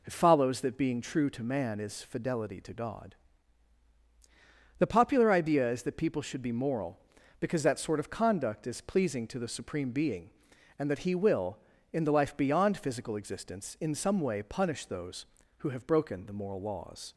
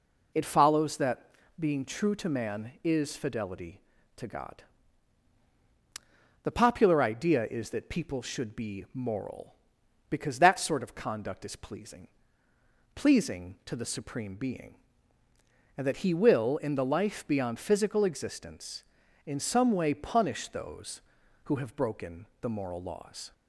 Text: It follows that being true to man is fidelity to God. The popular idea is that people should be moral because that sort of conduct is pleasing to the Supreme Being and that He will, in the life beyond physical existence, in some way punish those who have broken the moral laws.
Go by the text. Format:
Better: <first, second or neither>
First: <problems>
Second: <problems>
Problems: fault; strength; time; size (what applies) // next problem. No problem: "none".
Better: first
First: none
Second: pauses between "that" and "being"; slight; at 1.2 s; 0.30 s long // says "pleasing" twice; at 12.9 s // pauses between "broken" and "the"; slight; at 22.2 s; 0.16 s long